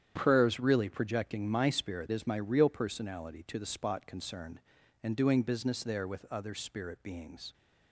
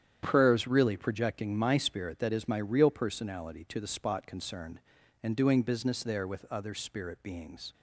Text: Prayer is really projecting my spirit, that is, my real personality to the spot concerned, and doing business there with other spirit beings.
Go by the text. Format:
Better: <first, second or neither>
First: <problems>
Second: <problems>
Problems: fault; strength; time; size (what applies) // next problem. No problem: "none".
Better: second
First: starts louder than the rest; strong; until 1.1 s; 9 dB // skips "that"; at 2.1 s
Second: starts louder than the rest; strong; until 1.2 s; 9 dB